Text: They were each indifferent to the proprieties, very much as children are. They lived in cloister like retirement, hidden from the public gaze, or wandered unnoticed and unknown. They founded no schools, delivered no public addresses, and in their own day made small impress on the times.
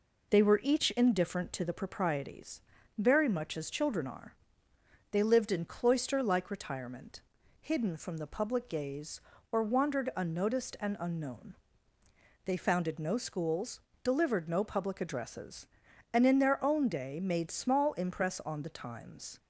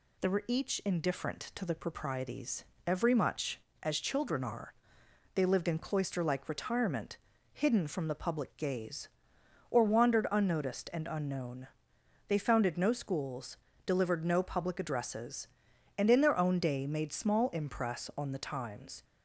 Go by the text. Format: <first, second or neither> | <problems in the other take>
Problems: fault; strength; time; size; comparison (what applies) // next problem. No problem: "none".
first | says "every" for "very"; at 2.8 s